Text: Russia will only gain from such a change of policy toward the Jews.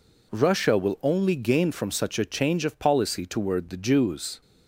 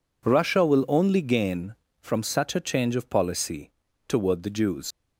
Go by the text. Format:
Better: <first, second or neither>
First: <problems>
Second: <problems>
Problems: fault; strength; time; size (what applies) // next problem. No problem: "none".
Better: first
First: none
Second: pauses between "policy" and "toward"; at 3.6 s; 0.38 s long // leaves "Jews" unfinished; at 4.9 s; 75 ms